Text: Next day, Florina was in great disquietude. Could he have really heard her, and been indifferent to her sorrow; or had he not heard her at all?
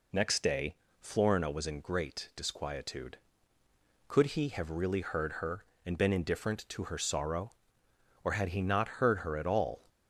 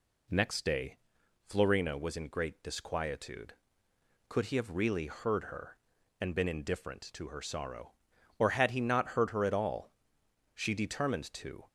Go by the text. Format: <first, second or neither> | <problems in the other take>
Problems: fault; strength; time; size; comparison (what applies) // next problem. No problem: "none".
first | goes on to say "She determined to"; noticeable; from 10.5 s on; 1.1 s long